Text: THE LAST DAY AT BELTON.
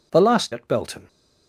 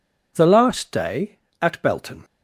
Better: second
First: skips "DAY"; at 0.5 s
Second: none

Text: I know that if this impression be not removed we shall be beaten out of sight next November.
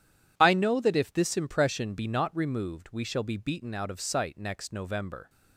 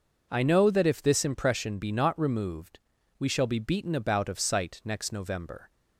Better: first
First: none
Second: pauses between "removed" and "we"; at 2.8 s; 0.38 s long // says "about" for "out"; at 3.9 s

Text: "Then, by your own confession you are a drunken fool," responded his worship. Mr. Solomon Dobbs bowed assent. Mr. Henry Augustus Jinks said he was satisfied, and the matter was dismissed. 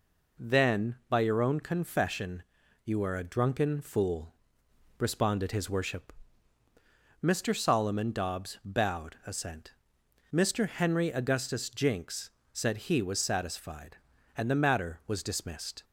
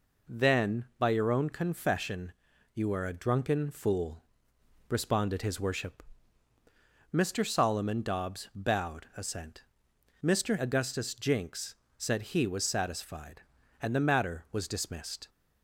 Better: first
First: pauses between "confession" and "you"; at 2.4 s; 0.40 s long // pauses between "Jinks" and "said"; slight; at 12.3 s; 0.20 s long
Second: pauses between "confession" and "you"; at 2.3 s; 0.40 s long // skips "Henry"; at 10.5 s // pauses between "Jinks" and "said"; slight; at 11.7 s; 0.20 s long

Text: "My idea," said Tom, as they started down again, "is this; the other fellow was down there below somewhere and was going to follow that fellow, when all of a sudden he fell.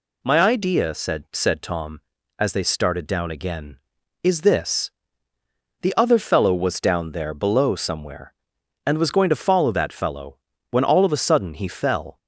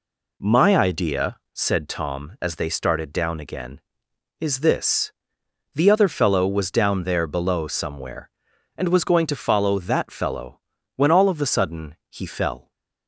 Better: second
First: says "said" twice; at 1.3 s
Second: none

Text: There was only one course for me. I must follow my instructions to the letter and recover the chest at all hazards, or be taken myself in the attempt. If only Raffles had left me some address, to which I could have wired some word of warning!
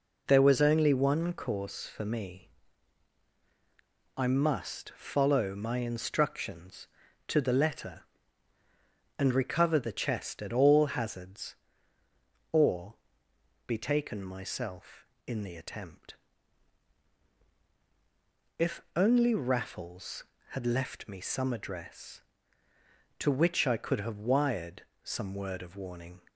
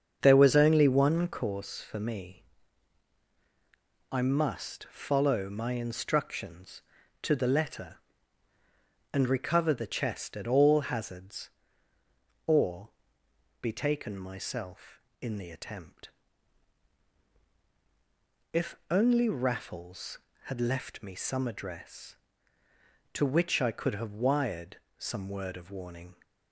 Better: first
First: pauses between "or" and "be"; noticeable; at 12.9 s; 0.74 s long // pauses between "wired" and "some"; slight; at 24.8 s; 0.22 s long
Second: starts louder than the rest; until 1.5 s; 7 dB // pauses between "or" and "be"; noticeable; at 12.8 s; 0.74 s long // pauses between "wired" and "some"; slight; at 24.7 s; 0.22 s long

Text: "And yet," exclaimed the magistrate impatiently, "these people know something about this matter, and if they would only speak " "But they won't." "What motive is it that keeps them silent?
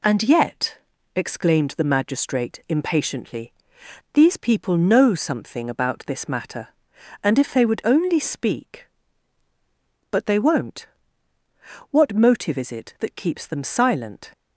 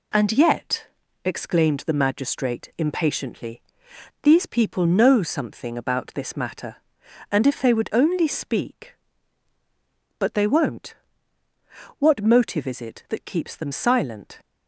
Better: neither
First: none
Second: none

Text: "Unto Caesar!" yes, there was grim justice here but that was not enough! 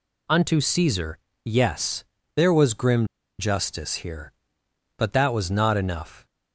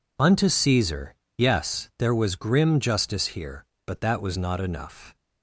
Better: second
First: pauses between "grim" and "justice"; slight; at 3.0 s; 0.32 s long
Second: none

